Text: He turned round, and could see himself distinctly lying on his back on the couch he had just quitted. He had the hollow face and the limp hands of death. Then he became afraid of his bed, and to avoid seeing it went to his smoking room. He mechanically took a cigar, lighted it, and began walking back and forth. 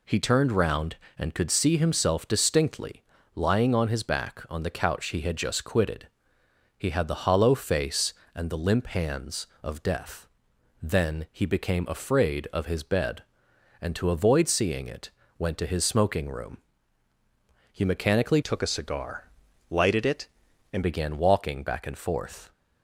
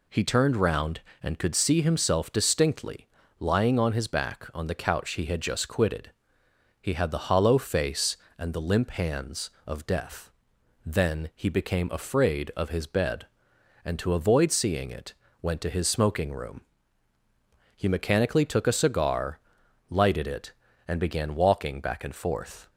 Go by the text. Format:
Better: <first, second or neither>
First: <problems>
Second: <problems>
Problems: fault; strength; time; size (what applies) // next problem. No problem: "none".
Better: second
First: pauses between "distinctly" and "lying"; slight; at 3.0 s; 0.36 s long // pauses between "it" and "went"; slight; at 15.0 s; 0.28 s long // changes voice from "took" to "and"; from 18.4 to 20.8 s; 2.4 s long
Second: pauses between "distinctly" and "lying"; slight; at 3.0 s; 0.36 s long // pauses between "it" and "went"; slight; at 15.1 s; 0.28 s long